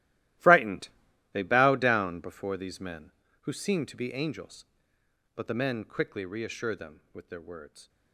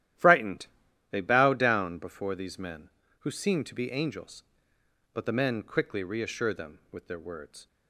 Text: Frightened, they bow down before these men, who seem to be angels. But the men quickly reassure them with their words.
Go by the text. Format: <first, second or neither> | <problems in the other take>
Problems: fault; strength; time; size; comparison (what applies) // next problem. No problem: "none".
second | gets quieter; strong; throughout; 16 dB // starts louder than the rest; strong; until 1.8 s; 15 dB; strong in the second